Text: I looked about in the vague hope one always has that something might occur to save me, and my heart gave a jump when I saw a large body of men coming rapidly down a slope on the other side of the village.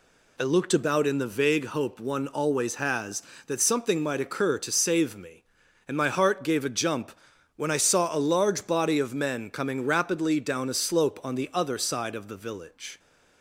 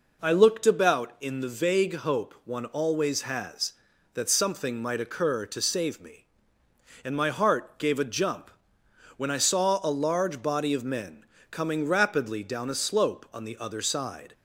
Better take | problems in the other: first | pauses between "jump" and "when"; noticeable; at 8.5 s; 0.64 s long; also in the first // pauses between "men" and "coming"; slight; at 11.2 s; 0.26 s long // stops before "of the village"; at 14.3 s

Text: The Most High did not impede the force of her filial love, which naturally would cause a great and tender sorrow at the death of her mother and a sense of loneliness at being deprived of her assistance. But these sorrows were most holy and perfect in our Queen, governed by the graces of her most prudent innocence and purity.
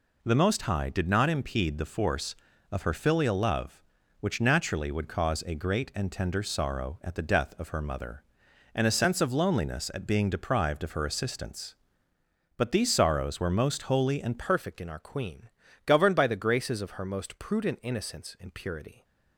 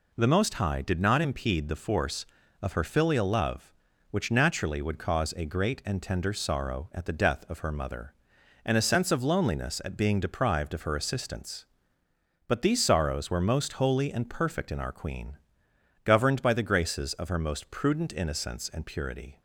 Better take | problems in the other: second | changes voice at "perfect"; from 14.3 s on; 4.7 s long

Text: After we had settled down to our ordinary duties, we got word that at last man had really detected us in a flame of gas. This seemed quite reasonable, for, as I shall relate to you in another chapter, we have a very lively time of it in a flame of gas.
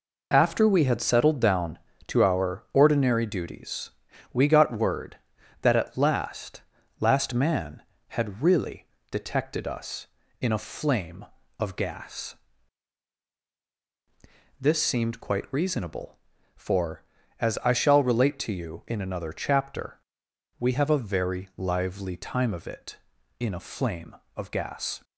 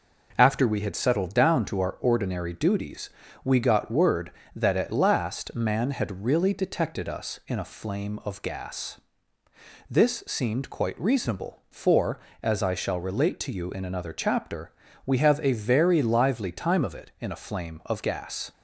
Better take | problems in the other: second | says "last" twice; at 7.0 s // pauses between "really" and "detected"; slight; at 8.8 s; 0.24 s long

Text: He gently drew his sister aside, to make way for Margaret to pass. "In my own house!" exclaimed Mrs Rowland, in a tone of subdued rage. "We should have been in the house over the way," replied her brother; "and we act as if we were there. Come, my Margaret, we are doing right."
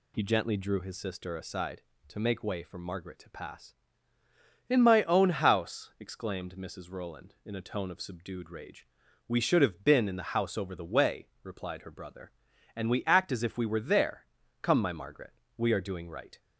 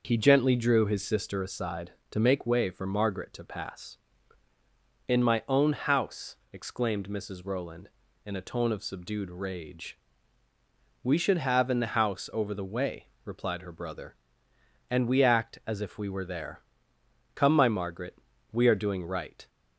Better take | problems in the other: first | starts louder than the rest; noticeable; until 1.0 s; 6 dB // skips "been"; at 11.7 s

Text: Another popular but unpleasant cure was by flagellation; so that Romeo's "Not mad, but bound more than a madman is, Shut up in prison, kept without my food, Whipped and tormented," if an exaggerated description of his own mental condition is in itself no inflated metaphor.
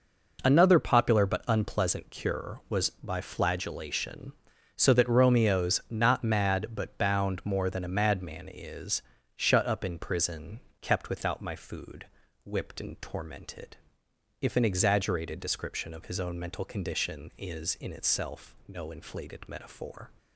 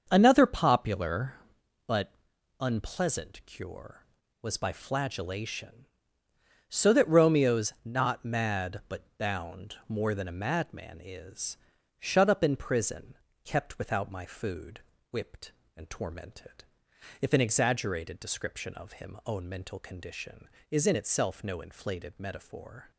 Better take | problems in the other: first | starts louder than the rest; until 1.1 s; 6.5 dB // pauses between "but" and "unpleasant"; noticeable; at 2.1 s; 0.48 s long // pauses between "but" and "bound"; slight; at 9.0 s; 0.16 s long // says "him" for "his"; at 19.0 s

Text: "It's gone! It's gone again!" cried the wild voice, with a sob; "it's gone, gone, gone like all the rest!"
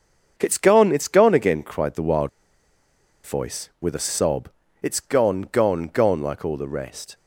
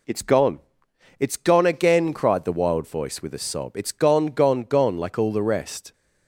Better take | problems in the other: second | starts louder than the rest; until 1.3 s; 6.5 dB // pauses between "wild" and "voice"; noticeable; at 2.2 s; 0.94 s long

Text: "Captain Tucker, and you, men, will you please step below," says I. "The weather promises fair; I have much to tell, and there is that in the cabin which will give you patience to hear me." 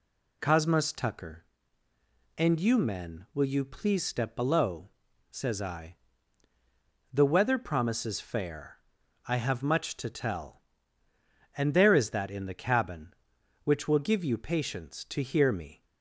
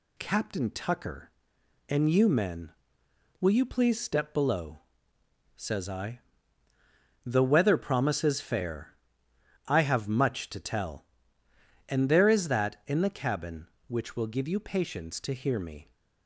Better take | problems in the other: second | says "Cosmos" for "Captain"; at 0.3 s

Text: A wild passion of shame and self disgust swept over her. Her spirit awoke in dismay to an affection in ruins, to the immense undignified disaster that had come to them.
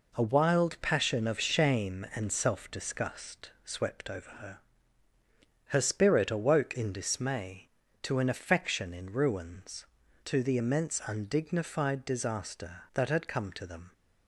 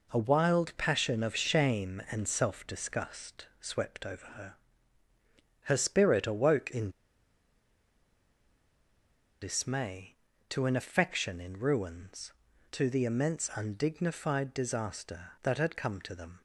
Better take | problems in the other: first | pauses between "disgust" and "swept"; slight; at 3.4 s; 0.16 s long; slight in the first // pauses between "in" and "dismay"; strong; at 6.8 s; 2.5 s long

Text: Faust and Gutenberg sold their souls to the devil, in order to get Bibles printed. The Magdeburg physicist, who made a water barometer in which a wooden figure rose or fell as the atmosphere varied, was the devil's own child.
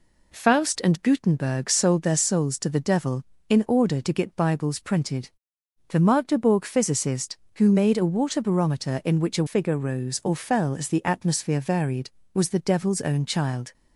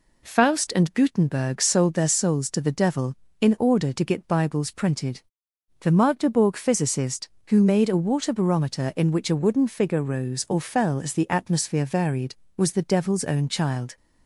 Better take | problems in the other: second | skips "wooden"; at 9.4 s

